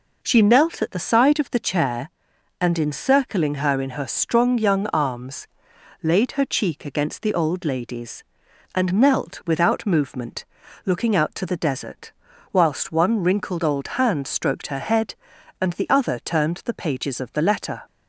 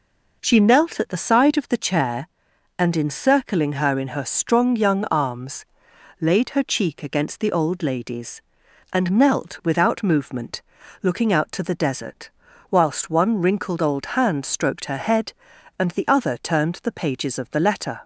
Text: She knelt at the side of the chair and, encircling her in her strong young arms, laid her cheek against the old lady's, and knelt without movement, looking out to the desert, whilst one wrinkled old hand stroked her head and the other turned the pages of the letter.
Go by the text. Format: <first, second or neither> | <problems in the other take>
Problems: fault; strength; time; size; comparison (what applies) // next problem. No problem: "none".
neither | none